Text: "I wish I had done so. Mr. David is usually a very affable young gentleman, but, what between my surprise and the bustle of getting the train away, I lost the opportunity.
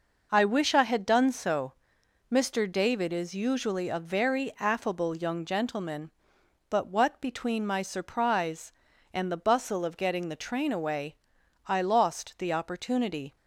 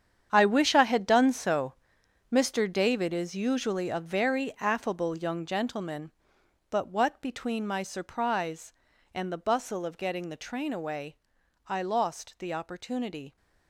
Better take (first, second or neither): first